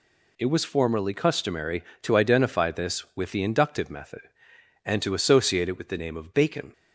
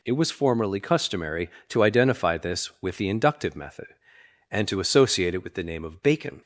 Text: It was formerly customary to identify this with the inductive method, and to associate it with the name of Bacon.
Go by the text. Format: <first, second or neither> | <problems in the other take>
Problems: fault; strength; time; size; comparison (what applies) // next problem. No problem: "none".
neither | none